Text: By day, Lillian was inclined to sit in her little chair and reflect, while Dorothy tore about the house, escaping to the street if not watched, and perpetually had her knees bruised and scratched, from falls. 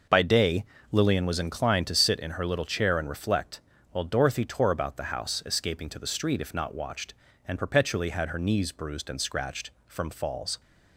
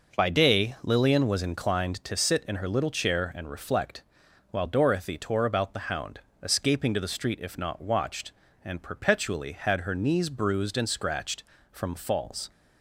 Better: first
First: none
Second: says "hound" for "house"; at 5.8 s

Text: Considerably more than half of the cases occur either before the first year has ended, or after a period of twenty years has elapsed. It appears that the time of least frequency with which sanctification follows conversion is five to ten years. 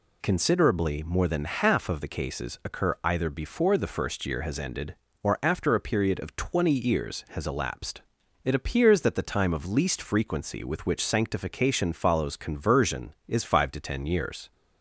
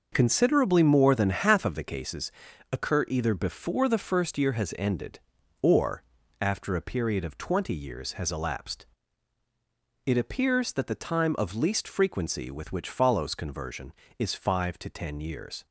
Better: first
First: none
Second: pauses between "cases" and "occur"; at 2.3 s; 0.40 s long // pauses between "or" and "after"; slight; at 6.0 s; 0.36 s long // skips "sanctification"; at 12.8 s

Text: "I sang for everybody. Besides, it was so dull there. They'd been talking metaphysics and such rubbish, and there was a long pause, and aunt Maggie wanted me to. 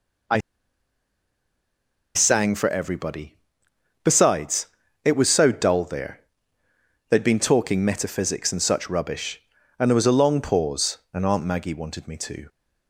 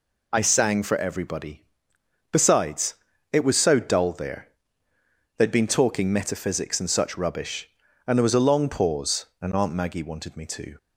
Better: second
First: pauses between "I" and "sang"; strong; at 0.3 s; 1.7 s long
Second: none

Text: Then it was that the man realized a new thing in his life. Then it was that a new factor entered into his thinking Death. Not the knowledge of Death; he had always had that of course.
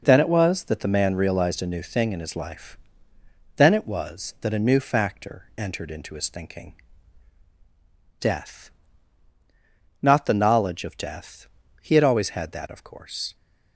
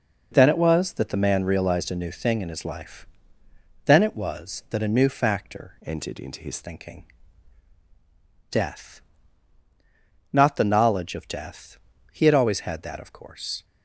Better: first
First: pauses between "thinking" and "Death"; strong; at 6.7 s; 1.4 s long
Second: changes voice from "entered" to "his"; from 5.8 to 6.5 s; 0.7 s long // pauses between "thinking" and "Death"; strong; at 7.0 s; 1.4 s long

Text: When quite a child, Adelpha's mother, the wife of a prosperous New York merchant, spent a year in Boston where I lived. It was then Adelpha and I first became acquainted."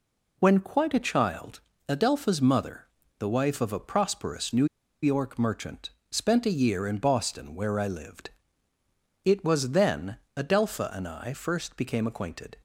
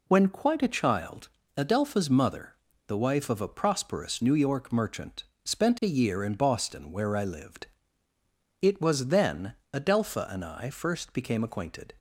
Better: second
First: pauses between "New" and "York"; at 4.6 s; 0.37 s long // pauses between "then" and "Adelpha"; slight; at 10.1 s; 0.20 s long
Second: pauses between "then" and "Adelpha"; slight; at 9.5 s; 0.20 s long

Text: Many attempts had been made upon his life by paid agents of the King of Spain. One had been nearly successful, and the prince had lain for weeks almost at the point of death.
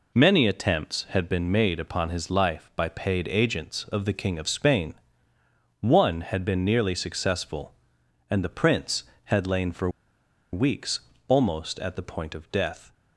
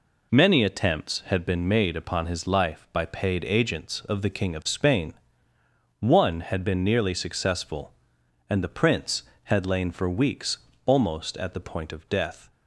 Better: second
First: pauses between "for" and "weeks"; noticeable; at 9.9 s; 0.61 s long // pauses between "weeks" and "almost"; slight; at 11.0 s; 0.26 s long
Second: pauses between "weeks" and "almost"; slight; at 10.5 s; 0.26 s long

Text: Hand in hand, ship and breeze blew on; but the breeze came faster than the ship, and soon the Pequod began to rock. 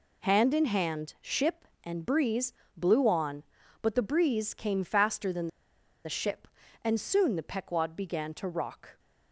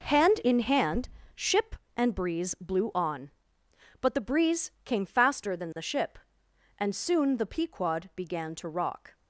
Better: second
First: pauses between "breeze" and "blew"; slight; at 2.5 s; 0.24 s long // pauses between "than" and "the"; noticeable; at 5.4 s; 0.57 s long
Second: none

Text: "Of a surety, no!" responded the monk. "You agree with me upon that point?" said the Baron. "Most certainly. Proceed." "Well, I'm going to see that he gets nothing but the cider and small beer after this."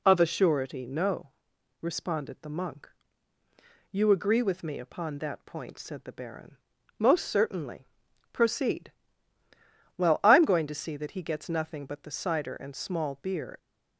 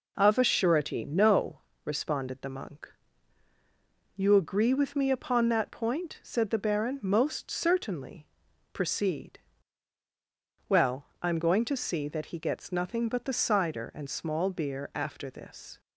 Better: second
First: stops before "after this"; at 13.5 s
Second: none

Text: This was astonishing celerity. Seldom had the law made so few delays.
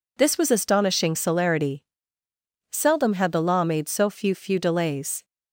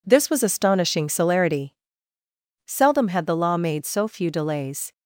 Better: second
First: says "few" twice; at 4.3 s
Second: none

